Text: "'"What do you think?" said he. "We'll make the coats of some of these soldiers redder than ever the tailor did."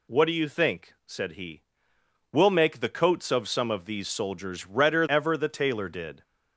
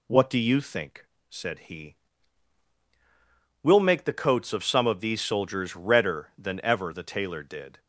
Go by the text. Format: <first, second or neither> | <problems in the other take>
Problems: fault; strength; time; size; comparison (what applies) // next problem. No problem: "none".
second | skips "than"; at 5.0 s